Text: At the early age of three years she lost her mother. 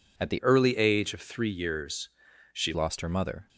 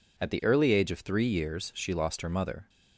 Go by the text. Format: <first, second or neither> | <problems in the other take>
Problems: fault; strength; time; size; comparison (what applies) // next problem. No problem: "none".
second | changes voice from "early" to "she"; from 0.4 to 2.7 s; 2.3 s long // pauses between "years" and "she"; at 2.0 s; 0.44 s long